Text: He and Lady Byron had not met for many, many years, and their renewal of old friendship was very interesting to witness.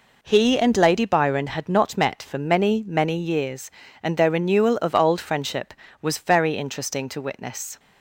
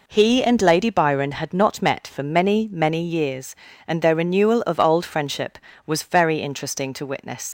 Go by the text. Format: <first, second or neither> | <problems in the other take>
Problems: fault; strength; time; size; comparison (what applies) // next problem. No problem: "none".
first | leaves "witness" unfinished; at 7.4 s; 110 ms